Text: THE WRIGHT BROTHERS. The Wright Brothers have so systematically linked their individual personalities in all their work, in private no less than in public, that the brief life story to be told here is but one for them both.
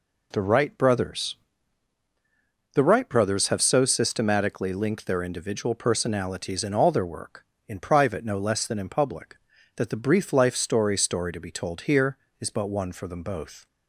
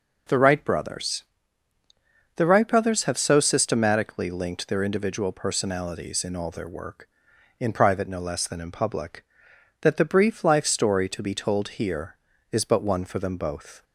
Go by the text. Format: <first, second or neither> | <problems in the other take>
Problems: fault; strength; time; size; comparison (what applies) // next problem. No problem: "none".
second | says "story" twice; at 10.9 s